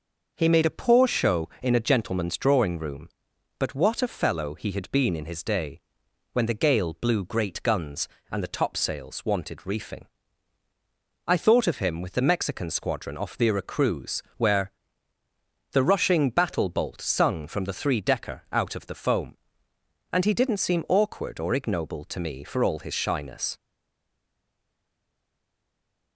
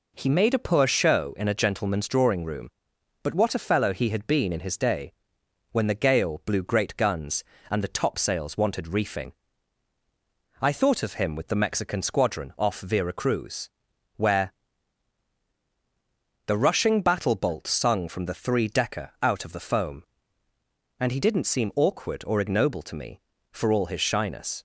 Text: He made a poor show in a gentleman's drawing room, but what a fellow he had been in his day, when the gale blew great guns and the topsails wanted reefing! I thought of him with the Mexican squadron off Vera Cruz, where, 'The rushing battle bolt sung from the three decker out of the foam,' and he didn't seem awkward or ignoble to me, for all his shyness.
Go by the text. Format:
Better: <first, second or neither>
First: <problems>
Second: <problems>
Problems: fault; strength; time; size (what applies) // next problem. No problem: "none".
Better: second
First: stays silent after the last word; strong; from 23.5 s on; 2.6 s long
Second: none